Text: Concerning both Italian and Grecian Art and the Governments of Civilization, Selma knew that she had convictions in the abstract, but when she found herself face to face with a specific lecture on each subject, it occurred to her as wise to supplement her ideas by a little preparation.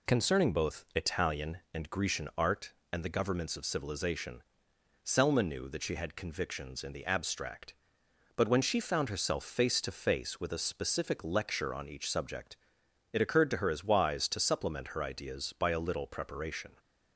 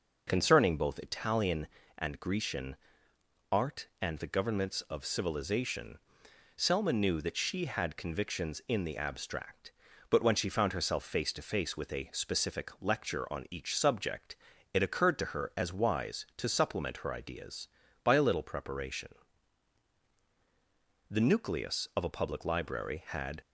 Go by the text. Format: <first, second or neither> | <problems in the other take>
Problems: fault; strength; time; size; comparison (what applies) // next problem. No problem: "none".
first | pauses between "Grecian" and "Art"; noticeable; at 2.7 s; 0.74 s long // goes on to say "The nucleus of a public library had"; strong; from 21.1 s on; 2.3 s long